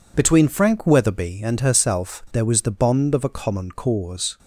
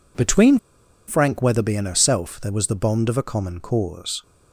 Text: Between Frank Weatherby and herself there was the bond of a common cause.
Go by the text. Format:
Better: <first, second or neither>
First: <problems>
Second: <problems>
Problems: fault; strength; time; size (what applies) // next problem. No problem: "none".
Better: first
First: none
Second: pauses between "Between" and "Frank"; noticeable; at 0.5 s; 0.49 s long